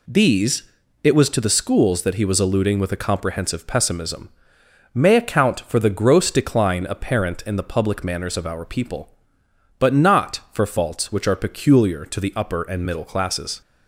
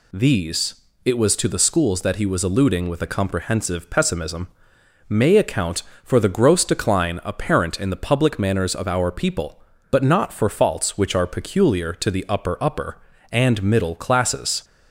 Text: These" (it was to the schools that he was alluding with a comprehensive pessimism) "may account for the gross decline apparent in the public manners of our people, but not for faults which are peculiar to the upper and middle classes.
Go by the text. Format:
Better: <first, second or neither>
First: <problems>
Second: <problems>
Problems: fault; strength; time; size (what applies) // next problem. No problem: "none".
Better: first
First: none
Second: says "upper" twice; at 12.6 s